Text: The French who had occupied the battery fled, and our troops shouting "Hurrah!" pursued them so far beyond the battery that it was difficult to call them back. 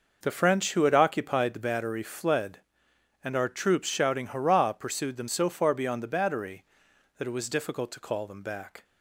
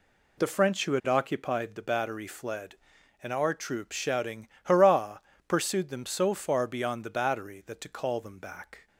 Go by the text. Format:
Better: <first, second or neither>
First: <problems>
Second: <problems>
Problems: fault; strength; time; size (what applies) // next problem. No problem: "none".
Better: first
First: none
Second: pauses between "shouting" and "Hurrah"; slight; at 4.4 s; 0.16 s long // skips "it was difficult"; at 7.7 s